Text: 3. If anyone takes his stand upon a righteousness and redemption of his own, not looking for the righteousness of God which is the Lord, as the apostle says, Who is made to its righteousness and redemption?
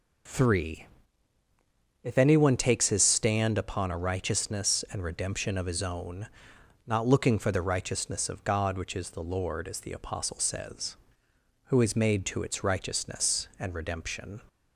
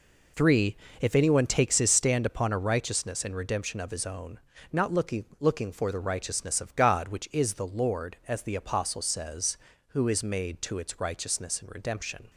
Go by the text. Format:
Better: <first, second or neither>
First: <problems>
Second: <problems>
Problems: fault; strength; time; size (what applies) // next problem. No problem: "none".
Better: first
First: none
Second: says "looking" twice; at 5.3 s